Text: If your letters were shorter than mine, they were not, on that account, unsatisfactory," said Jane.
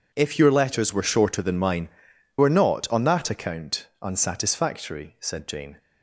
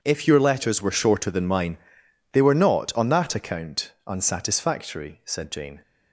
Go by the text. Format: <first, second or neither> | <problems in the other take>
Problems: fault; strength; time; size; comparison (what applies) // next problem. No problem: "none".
second | skips "they"; at 2.1 s